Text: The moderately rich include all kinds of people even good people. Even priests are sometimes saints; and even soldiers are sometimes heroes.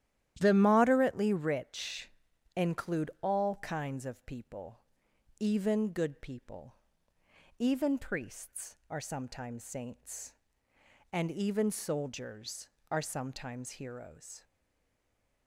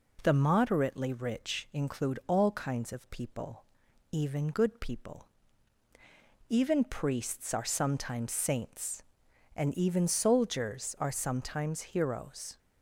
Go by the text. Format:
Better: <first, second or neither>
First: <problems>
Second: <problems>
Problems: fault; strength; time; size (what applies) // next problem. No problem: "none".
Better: second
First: starts louder than the rest; strong; until 1.4 s; 12 dB // pauses between "rich" and "include"; at 2.1 s; 0.44 s long // pauses between "people" and "even"; noticeable; at 4.7 s; 0.62 s long // stays silent after the last word; from 14.4 s on; 1.0 s long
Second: pauses between "people" and "even"; noticeable; at 3.6 s; 0.48 s long